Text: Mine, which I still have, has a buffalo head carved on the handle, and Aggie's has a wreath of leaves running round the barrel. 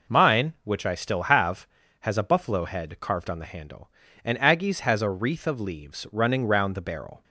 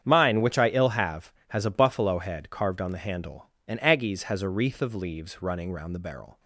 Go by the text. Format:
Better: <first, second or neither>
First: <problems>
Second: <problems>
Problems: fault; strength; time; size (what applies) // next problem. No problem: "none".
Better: first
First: none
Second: starts louder than the rest; strong; until 1.0 s; 8.5 dB // says "ill" for "still"; at 0.6 s